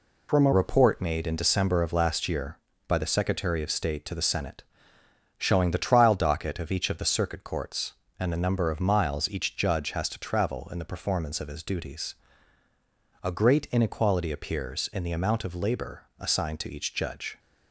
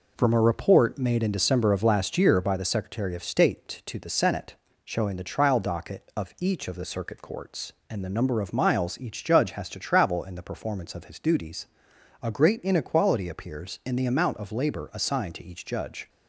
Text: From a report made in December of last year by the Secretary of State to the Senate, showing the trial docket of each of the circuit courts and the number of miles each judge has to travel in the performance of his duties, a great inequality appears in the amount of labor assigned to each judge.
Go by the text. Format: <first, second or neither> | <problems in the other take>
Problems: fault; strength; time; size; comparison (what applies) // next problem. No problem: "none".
second | changes voice at "report"; from 0.5 s on; 16.8 s long // pauses between "labor" and "assigned"; slight; at 16.0 s; 0.16 s long